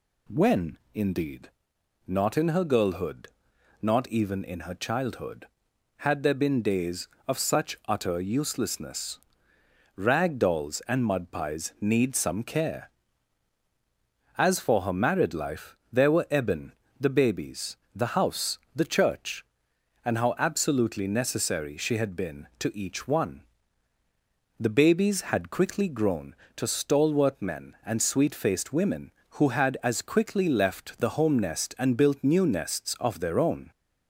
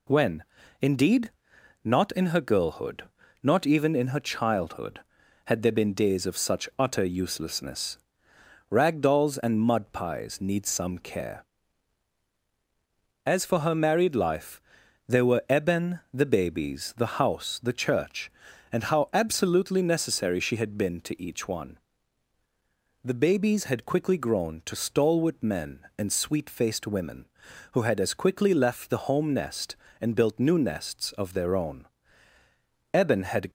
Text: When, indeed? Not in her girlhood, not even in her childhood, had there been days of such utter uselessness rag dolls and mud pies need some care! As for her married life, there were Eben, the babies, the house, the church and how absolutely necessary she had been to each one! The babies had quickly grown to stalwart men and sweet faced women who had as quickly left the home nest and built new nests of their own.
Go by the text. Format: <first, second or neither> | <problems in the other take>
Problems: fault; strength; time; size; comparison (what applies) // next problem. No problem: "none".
first | pauses between "uselessness" and "rag"; noticeable; at 7.9 s; 0.72 s long; noticeable in the first // goes on to say "Eben had"; from 32.9 s on; 0.58 s long